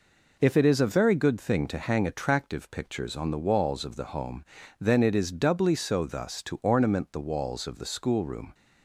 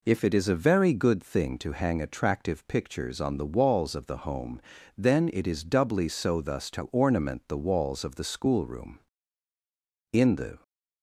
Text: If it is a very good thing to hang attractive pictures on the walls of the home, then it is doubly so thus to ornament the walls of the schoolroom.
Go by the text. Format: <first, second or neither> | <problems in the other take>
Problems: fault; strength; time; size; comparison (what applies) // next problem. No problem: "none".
first | goes on to say "In the"; from 10.1 s on; 0.50 s long